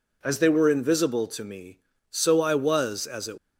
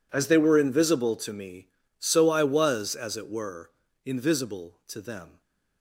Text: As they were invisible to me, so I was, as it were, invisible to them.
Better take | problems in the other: second | stops before "were invisible to them"; at 3.3 s

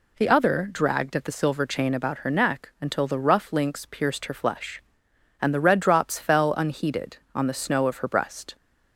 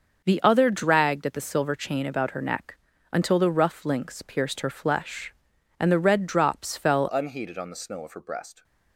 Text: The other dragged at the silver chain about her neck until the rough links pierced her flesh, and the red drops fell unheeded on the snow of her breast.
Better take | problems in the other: first | starts louder than the rest; noticeable; until 1.2 s; 6 dB // pauses between "neck" and "until"; slight; at 2.7 s; 0.34 s long // changes voice at "unheeded"; from 7.1 s on; 1.5 s long

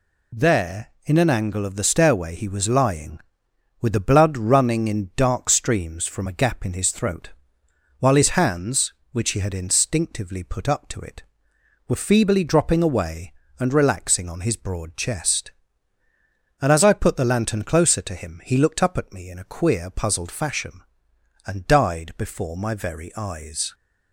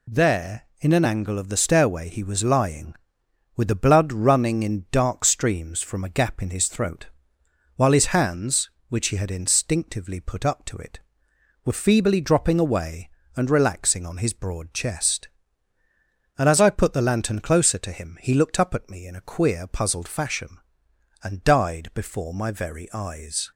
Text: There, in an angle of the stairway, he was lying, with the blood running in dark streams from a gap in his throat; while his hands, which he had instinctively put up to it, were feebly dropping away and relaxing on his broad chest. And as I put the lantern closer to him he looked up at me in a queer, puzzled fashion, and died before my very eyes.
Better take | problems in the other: neither | none

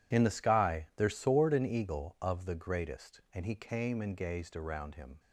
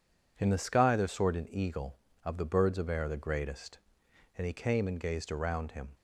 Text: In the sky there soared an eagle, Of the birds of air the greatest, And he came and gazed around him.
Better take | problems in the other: second | skips "the birds of air"; at 2.4 s

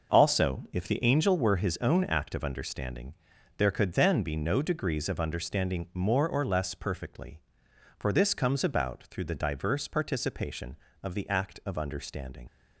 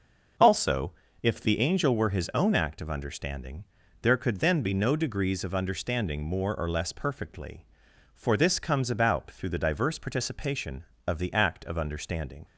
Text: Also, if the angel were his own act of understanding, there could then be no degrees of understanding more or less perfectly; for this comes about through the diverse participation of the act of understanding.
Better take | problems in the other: second | starts louder than the rest; noticeable; until 1.2 s; 6 dB; also in the second // leaves "understanding" unfinished; at 12.4 s; 60 ms

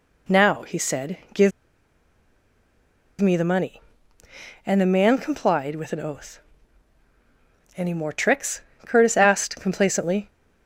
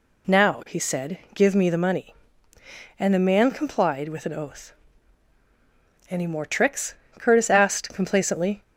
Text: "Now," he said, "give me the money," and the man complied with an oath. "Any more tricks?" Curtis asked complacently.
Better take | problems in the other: second | pauses between "give" and "me"; strong; at 1.5 s; 1.6 s long

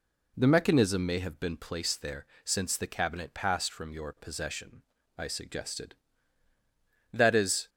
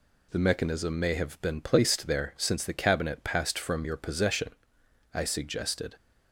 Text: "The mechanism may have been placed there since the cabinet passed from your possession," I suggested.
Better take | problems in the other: second | pauses between "there" and "since"; slight; at 2.2 s; 0.18 s long // goes on to say "That is"; from 7.1 s on; 0.58 s long

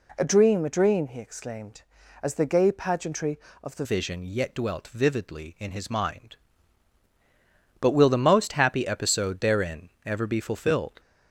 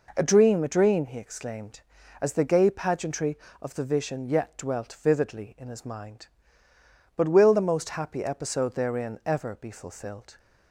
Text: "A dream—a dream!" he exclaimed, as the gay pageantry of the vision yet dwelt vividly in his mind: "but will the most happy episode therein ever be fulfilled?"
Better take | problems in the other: second | changes voice at "vision"; from 3.8 s on; 7.1 s long // pauses between "therein" and "ever"; slight; at 9.8 s; 0.16 s long

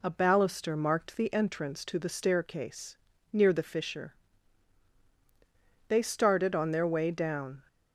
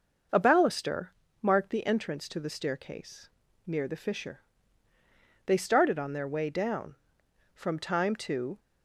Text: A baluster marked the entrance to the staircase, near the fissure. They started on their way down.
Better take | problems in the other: first | pauses between "baluster" and "marked"; slight; at 1.0 s; 0.32 s long // goes on to say "From time to"; noticeable; from 7.5 s on; 1.0 s long

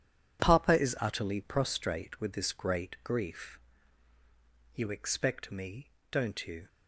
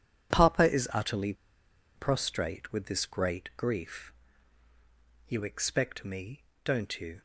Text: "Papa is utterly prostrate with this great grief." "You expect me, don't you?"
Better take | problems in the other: first | pauses between "utterly" and "prostrate"; noticeable; at 1.3 s; 0.62 s long

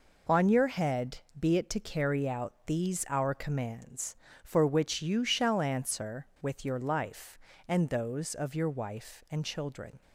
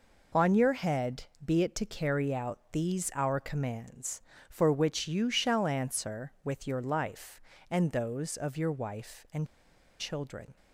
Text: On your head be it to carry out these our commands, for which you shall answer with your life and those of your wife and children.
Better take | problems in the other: first | pauses between "head" and "be"; slight; at 1.2 s; 0.20 s long; slight in the first // pauses between "and" and "children"; noticeable; at 9.4 s; 0.54 s long

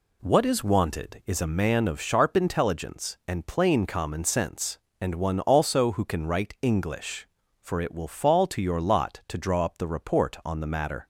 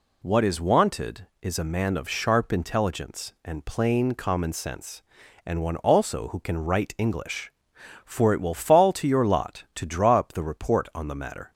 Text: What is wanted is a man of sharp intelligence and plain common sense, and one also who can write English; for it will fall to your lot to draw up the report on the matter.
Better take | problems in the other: neither | none

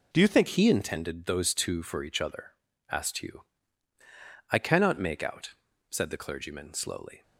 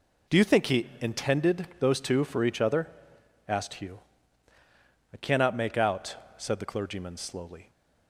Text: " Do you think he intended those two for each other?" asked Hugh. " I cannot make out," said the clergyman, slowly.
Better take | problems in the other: second | changes voice at "he"; from 0.4 s on; 6.8 s long

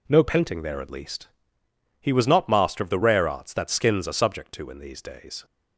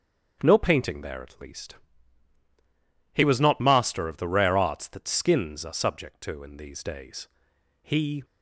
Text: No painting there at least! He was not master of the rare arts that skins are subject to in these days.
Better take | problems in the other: first | starts louder than the rest; strong; until 1.4 s; 7.5 dB // goes on to say "He"; slight; from 7.8 s on; 0.42 s long

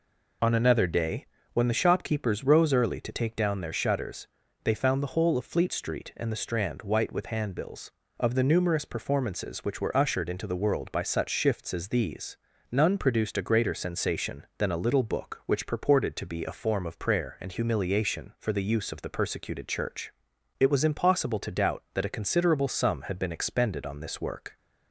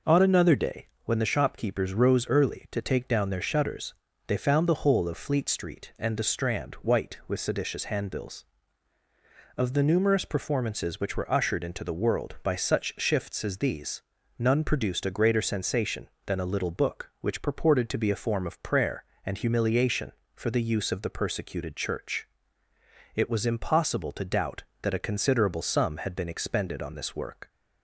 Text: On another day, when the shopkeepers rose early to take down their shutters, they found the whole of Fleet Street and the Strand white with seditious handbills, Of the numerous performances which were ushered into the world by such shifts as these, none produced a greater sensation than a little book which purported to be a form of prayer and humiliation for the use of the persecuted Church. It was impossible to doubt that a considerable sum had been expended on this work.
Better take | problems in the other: second | skips "seditious"; at 7.2 s

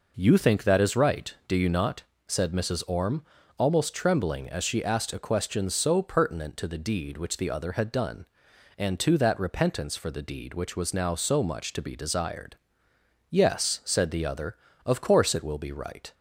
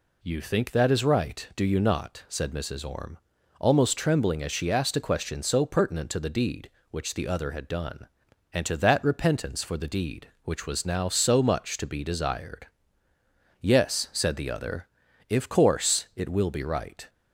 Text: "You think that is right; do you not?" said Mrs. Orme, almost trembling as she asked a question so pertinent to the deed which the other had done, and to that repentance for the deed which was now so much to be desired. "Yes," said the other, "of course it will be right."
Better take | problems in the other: first | says "if" for "of"; at 15.2 s

